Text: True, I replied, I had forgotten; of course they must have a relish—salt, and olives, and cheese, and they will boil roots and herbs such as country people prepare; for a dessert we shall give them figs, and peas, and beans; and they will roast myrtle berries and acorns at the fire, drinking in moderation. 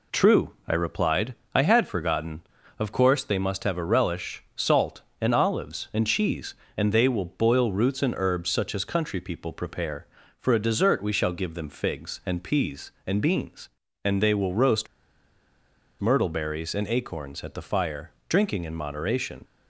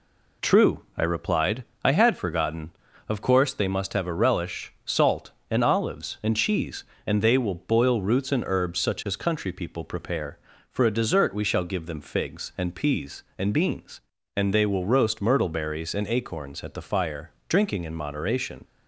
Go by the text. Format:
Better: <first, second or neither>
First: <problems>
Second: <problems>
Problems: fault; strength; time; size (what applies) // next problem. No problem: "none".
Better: second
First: pauses between "roast" and "myrtle"; at 14.8 s; 1.1 s long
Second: none